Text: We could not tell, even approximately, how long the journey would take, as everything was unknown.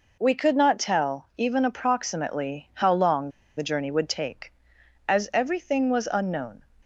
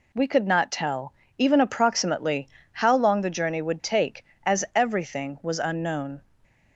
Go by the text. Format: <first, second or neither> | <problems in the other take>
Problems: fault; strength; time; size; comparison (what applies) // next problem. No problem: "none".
second | pauses between "long" and "the"; slight; at 3.2 s; 0.27 s long